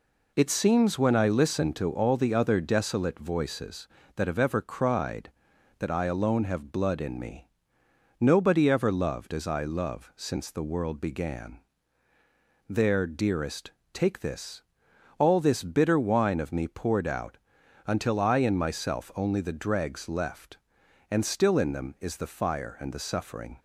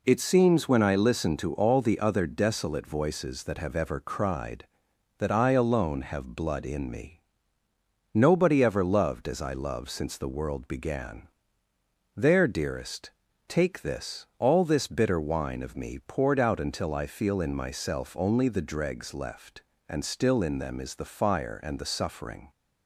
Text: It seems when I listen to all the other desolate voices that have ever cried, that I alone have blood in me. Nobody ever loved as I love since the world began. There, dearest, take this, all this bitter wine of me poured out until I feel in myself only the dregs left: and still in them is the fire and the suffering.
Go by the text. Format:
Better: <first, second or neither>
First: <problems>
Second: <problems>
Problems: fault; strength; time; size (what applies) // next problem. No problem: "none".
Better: second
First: pauses between "out" and "until"; noticeable; at 17.3 s; 0.48 s long // skips "feel"; at 18.3 s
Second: none